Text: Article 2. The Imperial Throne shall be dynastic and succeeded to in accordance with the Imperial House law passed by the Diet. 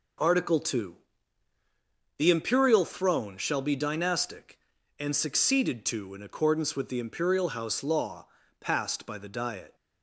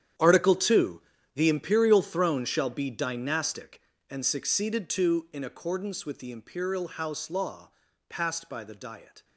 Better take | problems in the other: first | gets quieter; strong; throughout; 15 dB // pauses between "law" and "passed"; at 7.7 s; 0.38 s long; slight in the first

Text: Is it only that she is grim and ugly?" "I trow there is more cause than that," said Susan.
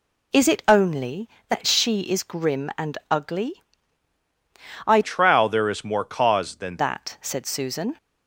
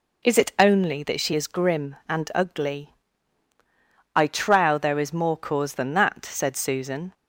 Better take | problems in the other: second | changes voice from "trow" to "than"; from 5.0 to 6.7 s; 1.7 s long

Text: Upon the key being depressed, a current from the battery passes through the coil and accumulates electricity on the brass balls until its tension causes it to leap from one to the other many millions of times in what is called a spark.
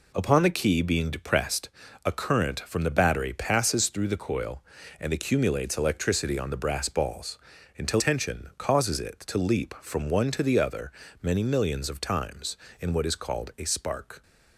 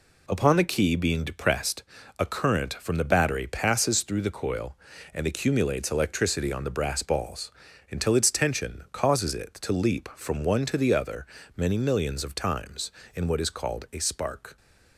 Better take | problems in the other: second | pauses between "balls" and "until"; at 7.3 s; 0.40 s long; also in the second // skips "its"; at 7.9 s // pauses between "other" and "many"; slight; at 10.9 s; 0.30 s long; slight in the second

